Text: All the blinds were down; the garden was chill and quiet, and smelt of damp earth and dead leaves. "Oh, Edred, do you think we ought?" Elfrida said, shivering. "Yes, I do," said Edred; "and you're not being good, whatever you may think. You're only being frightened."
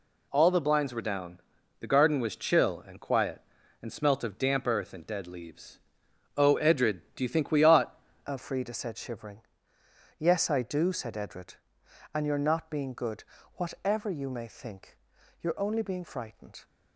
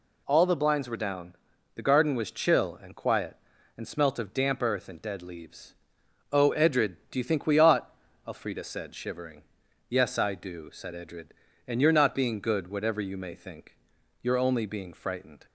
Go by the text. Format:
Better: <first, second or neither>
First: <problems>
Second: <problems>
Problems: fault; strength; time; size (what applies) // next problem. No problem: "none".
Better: second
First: changes voice at "Elfrida"; from 8.2 s on; 8.4 s long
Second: none